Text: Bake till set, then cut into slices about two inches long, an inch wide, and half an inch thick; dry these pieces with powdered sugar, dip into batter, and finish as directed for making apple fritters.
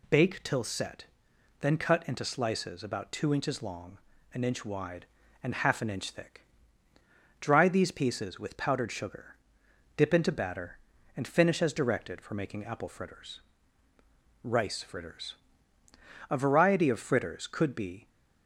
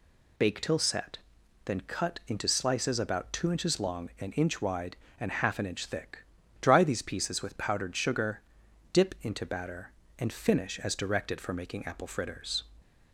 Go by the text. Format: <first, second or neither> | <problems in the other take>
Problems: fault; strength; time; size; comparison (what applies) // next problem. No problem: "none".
second | goes on to say "RICE FRITTERS A variety of fritters could be"; strong; from 14.4 s on; 3.6 s long